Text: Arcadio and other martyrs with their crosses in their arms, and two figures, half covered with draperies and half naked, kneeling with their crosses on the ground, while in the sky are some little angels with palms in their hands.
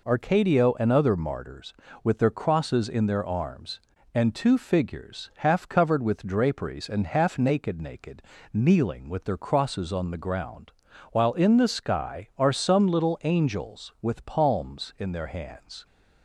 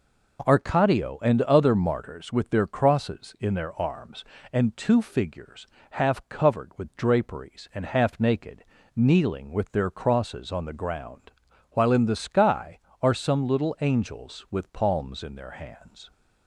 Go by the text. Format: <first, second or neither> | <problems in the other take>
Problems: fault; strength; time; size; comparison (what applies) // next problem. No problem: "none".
second | says "naked" twice; at 7.8 s